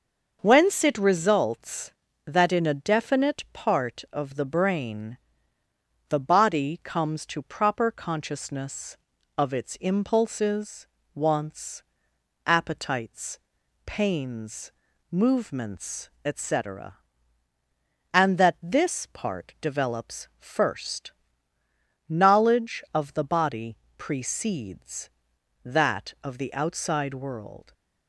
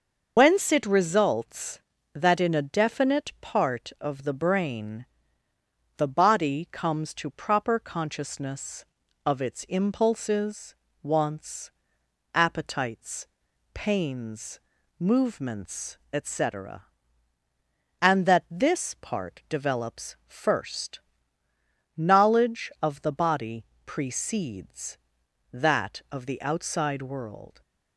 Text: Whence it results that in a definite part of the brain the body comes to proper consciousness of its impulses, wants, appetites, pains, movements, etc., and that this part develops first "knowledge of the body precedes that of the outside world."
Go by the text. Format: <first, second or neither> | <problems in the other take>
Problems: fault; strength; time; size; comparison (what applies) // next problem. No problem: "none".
first | loses the start of "Whence"; at 0.3 s; 80 ms // starts louder than the rest; noticeable; until 1.3 s; 6 dB; noticeable in the first // pauses between "brain" and "the"; noticeable; at 5.0 s; 0.90 s long; noticeable in the first // pauses between "first" and "knowledge"; noticeable; at 20.9 s; 0.96 s long; noticeable in the first // pauses between "body" and "precedes"; slight; at 23.6 s; 0.22 s long; slight in the first